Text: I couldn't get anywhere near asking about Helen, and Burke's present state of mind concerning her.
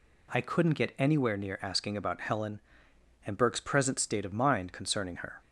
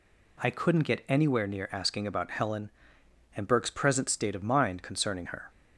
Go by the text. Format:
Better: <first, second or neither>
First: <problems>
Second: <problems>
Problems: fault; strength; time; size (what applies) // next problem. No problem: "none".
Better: neither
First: none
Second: none